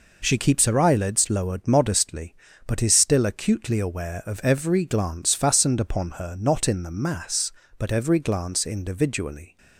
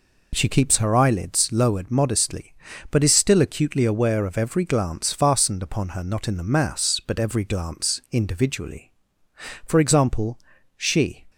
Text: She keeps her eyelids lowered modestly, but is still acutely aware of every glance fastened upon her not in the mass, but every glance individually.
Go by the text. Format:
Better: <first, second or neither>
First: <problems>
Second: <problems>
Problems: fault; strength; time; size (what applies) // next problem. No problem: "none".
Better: first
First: none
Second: goes on to say "For example she"; from 9.6 s on; 1.6 s long